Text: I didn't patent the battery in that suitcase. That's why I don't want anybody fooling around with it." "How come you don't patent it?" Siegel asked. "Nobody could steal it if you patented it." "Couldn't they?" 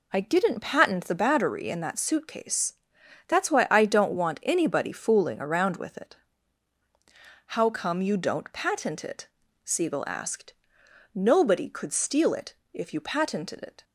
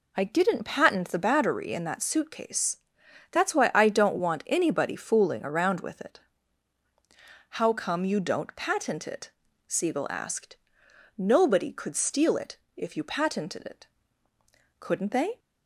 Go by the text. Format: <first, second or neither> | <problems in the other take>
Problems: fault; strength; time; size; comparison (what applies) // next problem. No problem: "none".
second | pauses between "it" and "if"; slight; at 12.5 s; 0.16 s long; slight in the second // stops before "Couldn't they"; at 13.8 s